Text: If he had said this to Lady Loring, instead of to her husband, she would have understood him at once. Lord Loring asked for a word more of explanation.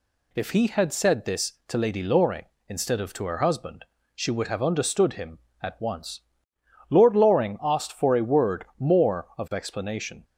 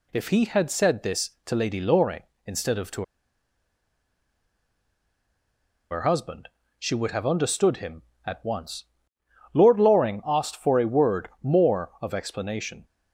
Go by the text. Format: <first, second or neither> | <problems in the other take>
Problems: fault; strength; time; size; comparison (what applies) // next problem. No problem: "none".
first | pauses between "to" and "her"; strong; at 3.0 s; 2.8 s long